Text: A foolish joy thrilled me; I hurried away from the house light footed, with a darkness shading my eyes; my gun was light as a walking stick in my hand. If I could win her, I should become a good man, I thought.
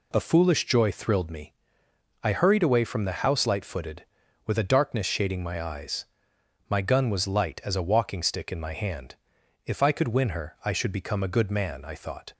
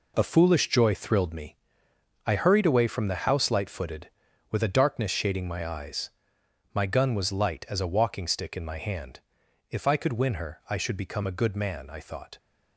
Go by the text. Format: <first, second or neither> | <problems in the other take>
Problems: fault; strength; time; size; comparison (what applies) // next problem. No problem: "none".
first | gets quieter; strong; throughout; 8.5 dB